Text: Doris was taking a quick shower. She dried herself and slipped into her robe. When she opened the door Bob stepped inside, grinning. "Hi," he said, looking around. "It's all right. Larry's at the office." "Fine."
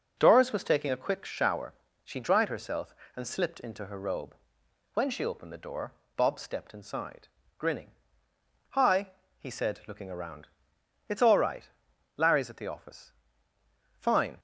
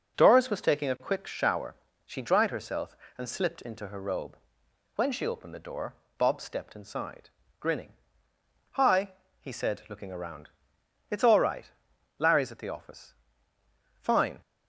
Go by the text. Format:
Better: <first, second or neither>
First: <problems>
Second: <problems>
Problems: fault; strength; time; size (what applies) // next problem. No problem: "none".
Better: neither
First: pauses between "door" and "Bob"; slight; at 5.9 s; 0.24 s long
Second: pauses between "door" and "Bob"; slight; at 5.9 s; 0.24 s long